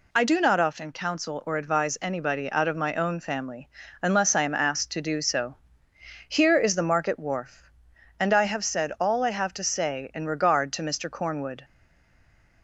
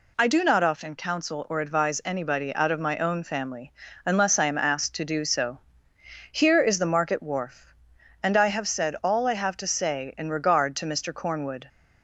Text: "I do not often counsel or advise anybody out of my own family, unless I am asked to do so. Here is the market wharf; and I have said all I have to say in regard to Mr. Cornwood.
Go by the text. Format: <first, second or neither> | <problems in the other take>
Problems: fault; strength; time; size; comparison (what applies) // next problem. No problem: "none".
second | stays silent after the last word; from 11.6 s on; 1.0 s long